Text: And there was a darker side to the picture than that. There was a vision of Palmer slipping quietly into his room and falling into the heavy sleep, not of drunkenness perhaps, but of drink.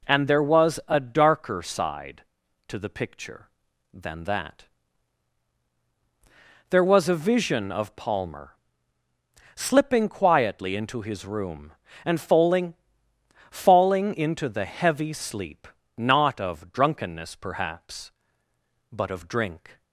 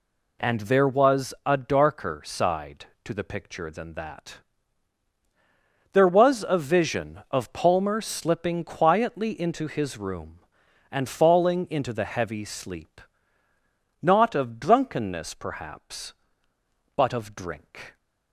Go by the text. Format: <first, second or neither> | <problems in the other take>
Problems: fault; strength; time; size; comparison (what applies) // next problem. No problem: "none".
second | pauses between "Palmer" and "slipping"; at 8.5 s; 1.0 s long // says "falling" twice; at 13.5 s